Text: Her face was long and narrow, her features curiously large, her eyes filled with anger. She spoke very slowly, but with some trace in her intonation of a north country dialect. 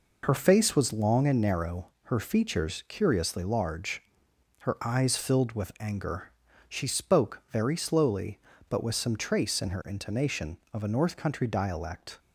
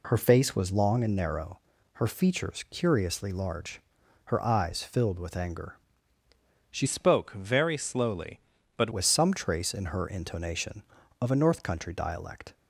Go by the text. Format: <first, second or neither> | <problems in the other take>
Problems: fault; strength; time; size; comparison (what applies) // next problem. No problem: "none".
first | changes voice from "spoke" to "but"; from 6.8 to 8.9 s; 2.1 s long